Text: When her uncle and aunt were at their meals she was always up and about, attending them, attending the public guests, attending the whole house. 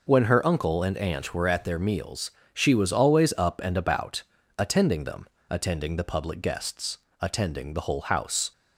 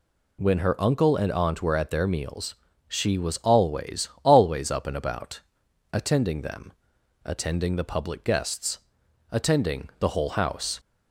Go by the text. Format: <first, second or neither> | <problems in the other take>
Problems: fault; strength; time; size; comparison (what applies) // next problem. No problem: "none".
first | pauses between "meals" and "she"; slight; at 2.5 s; 0.34 s long; slight in the first // says "always" twice; at 4.2 s